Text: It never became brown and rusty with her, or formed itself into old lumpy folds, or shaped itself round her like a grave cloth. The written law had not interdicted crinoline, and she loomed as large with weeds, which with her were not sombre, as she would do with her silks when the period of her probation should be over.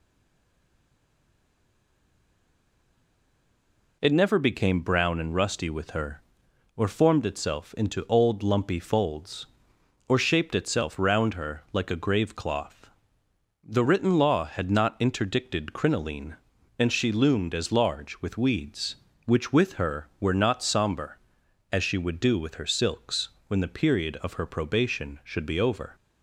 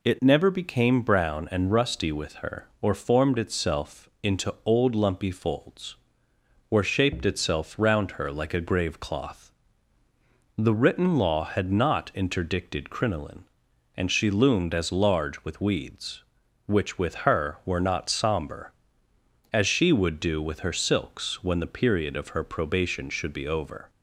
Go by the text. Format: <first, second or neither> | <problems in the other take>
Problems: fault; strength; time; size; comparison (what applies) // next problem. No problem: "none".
second | stays silent before the first word; strong; until 4.0 s; 4.0 s long // pauses between "silks" and "when"; slight; at 23.2 s; 0.18 s long